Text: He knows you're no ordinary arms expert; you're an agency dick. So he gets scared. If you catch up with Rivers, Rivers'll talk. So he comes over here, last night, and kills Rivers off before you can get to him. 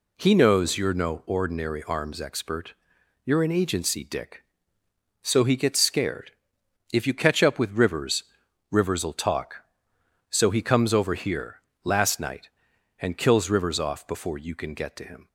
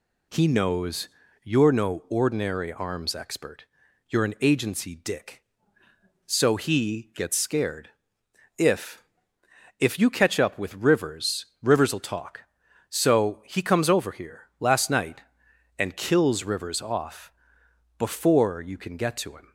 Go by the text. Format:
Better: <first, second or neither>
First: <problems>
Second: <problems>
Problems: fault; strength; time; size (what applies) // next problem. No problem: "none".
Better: first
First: none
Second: pauses between "knows" and "you're"; slight; at 1.0 s; 0.34 s long // says "If" twice; at 9.7 s // pauses between "off" and "before"; noticeable; at 17.3 s; 0.64 s long